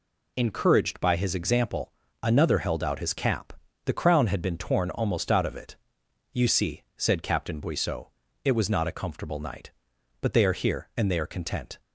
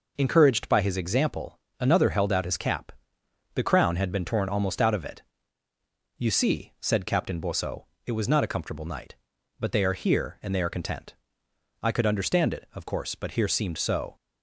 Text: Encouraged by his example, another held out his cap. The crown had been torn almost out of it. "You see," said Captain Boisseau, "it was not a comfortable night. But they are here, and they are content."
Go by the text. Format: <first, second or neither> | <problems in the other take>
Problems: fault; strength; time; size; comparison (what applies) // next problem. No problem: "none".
first | goes on to say "I could understand it of course but here seemed so"; strong; from 11.8 s on; 2.3 s long